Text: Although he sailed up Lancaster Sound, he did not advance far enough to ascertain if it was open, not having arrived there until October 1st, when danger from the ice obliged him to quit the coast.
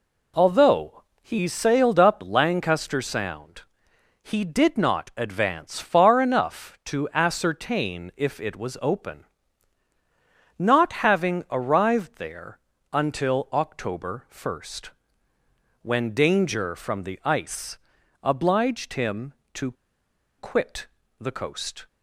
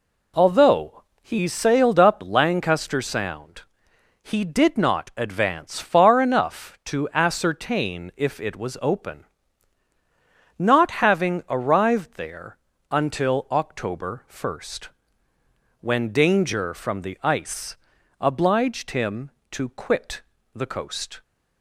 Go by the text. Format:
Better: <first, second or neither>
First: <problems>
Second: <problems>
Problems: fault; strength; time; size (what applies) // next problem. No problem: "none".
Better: second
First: pauses between "Although" and "he"; slight; at 1.0 s; 0.18 s long // pauses between "there" and "until"; slight; at 12.5 s; 0.32 s long // pauses between "ice" and "obliged"; at 17.7 s; 0.44 s long // pauses between "to" and "quit"; noticeable; at 19.7 s; 0.67 s long // pauses between "quit" and "the"; slight; at 20.8 s; 0.32 s long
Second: pauses between "Although" and "he"; slight; at 1.0 s; 0.18 s long // pauses between "there" and "until"; slight; at 12.5 s; 0.32 s long // pauses between "ice" and "obliged"; at 17.7 s; 0.42 s long // pauses between "quit" and "the"; slight; at 20.2 s; 0.32 s long